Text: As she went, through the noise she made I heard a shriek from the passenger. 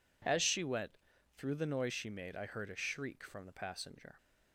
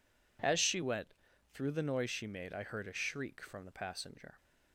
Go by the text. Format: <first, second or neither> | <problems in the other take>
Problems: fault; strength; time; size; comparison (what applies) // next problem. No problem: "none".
neither | none